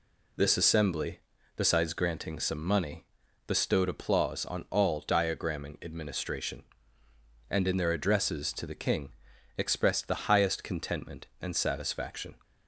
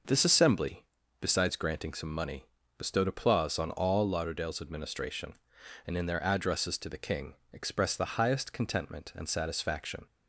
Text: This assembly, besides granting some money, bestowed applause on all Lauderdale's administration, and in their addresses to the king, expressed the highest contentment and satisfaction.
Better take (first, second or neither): second